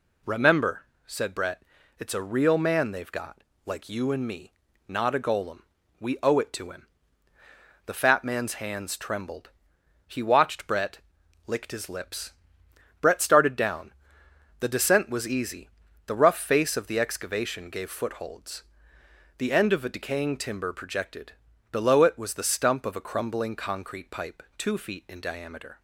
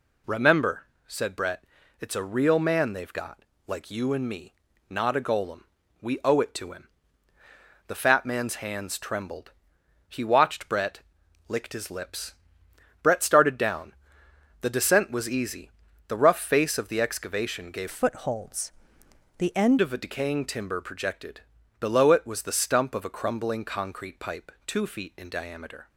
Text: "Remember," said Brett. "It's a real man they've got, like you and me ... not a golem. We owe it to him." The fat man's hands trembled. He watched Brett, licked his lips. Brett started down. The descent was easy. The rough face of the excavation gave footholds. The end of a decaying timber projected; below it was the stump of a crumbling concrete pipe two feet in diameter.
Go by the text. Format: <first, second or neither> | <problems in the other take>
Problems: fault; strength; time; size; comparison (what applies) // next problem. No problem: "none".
first | changes voice from "footholds" to "end"; from 17.8 to 19.7 s; 1.9 s long